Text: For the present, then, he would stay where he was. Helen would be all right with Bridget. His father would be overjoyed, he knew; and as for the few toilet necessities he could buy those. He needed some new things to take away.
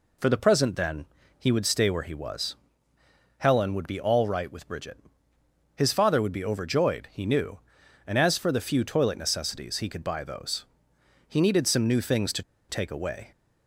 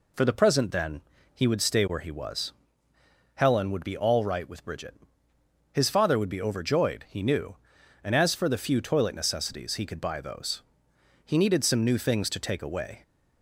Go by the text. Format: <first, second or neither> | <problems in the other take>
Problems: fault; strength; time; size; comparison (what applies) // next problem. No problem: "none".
second | pauses between "to" and "take"; slight; at 12.4 s; 0.27 s long